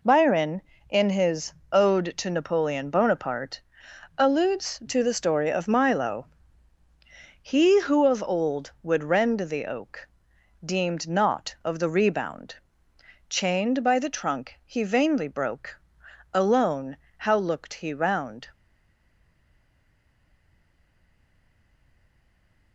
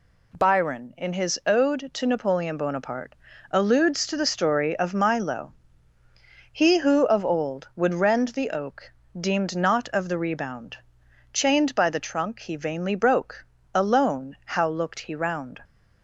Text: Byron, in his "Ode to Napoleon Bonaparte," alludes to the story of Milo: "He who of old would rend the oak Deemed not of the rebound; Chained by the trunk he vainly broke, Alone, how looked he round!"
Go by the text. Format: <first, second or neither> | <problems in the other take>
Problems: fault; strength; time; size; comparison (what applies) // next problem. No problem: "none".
second | pauses between "his" and "Ode"; slight; at 1.5 s; 0.18 s long // pauses between "oak" and "Deemed"; noticeable; at 10.0 s; 0.58 s long; slight in the second // stays silent after the last word; strong; from 18.5 s on; 4.2 s long